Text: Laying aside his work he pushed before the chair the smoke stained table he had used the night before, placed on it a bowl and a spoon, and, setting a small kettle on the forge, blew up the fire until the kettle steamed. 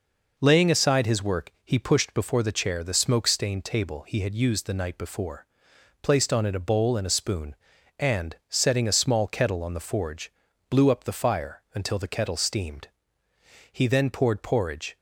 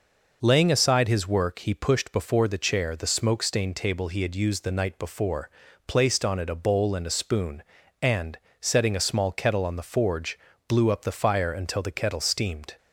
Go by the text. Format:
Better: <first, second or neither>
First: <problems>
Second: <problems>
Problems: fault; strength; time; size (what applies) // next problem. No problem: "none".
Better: second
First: goes on to say "He then poured porridge"; noticeable; from 13.7 s on; 1.2 s long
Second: none